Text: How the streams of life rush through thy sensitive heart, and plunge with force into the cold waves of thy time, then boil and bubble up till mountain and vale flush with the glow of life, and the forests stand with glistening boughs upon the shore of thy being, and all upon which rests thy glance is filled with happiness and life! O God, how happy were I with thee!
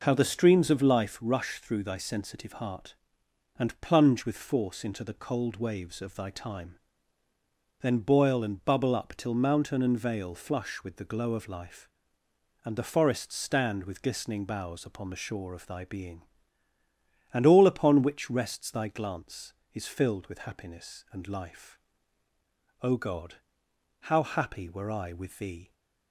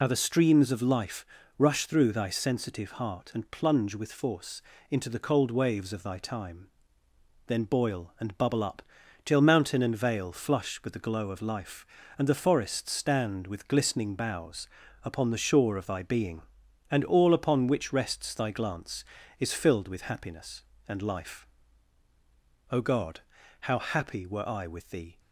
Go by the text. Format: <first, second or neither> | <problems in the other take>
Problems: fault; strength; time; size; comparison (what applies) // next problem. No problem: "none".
first | loses the start of "How"; at 0.0 s; 50 ms // pauses between "life" and "rush"; slight; at 1.2 s; 0.32 s long // pauses between "force" and "into"; slight; at 4.6 s; 0.30 s long // pauses between "up" and "till"; at 8.8 s; 0.42 s long // pauses between "boughs" and "upon"; slight; at 14.6 s; 0.36 s long